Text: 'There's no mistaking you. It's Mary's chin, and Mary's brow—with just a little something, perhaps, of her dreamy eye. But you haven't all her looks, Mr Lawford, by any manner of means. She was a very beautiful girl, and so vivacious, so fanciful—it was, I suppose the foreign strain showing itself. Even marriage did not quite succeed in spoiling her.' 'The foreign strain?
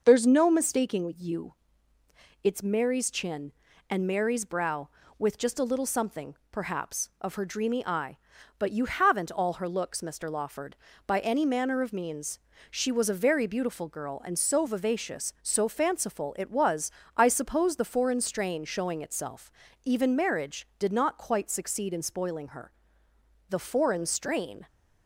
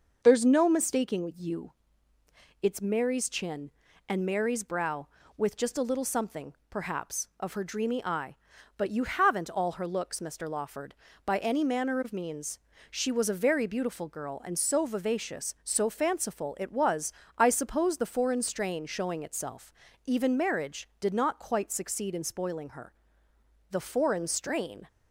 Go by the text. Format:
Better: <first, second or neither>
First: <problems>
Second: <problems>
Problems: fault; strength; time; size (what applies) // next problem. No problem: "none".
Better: neither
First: starts louder than the rest; noticeable; until 1.0 s; 6 dB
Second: starts louder than the rest; noticeable; until 1.2 s; 6 dB